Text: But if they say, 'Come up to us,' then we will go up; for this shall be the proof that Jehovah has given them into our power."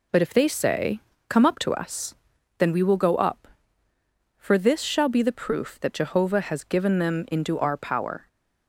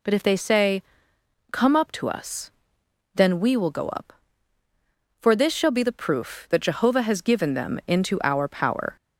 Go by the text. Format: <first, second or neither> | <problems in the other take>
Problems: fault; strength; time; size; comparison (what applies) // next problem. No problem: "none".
neither | none